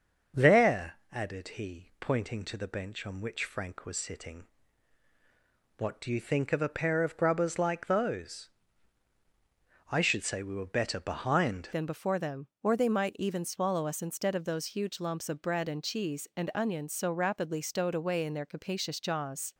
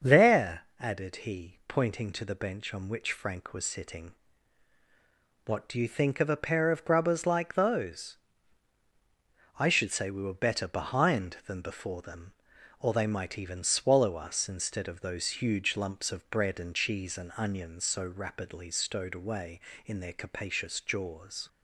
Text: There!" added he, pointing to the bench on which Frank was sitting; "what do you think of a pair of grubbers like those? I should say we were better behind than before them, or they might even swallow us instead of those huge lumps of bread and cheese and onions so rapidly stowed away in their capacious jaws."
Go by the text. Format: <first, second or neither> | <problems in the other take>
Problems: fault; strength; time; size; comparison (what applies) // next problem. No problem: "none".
second | starts louder than the rest; until 1.6 s; 6 dB; also in the second // changes voice at "than"; from 11.7 s on; 7.8 s long